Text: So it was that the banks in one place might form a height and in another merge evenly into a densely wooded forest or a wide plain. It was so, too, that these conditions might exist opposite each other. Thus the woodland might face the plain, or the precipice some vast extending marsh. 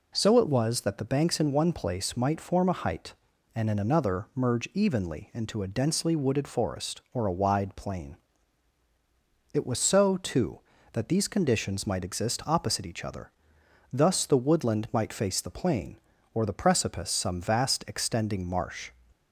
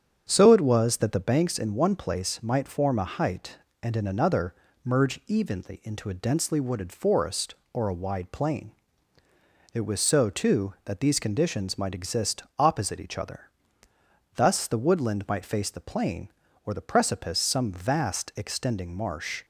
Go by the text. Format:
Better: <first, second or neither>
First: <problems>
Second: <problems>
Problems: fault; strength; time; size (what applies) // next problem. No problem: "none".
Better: first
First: none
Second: starts louder than the rest; strong; until 1.3 s; 8 dB // pauses between "another" and "merge"; slight; at 4.5 s; 0.30 s long // pauses between "exist" and "opposite"; slight; at 12.4 s; 0.16 s long